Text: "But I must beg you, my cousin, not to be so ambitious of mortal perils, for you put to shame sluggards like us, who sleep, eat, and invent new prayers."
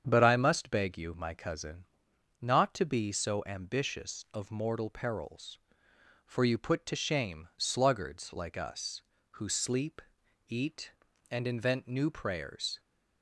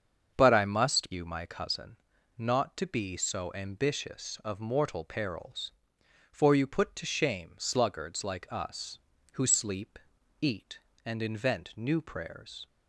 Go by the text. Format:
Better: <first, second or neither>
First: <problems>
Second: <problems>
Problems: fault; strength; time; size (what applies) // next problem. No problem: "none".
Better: first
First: starts louder than the rest; strong; until 1.0 s; 8 dB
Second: starts louder than the rest; strong; until 1.3 s; 7 dB // skips "beg"; at 1.1 s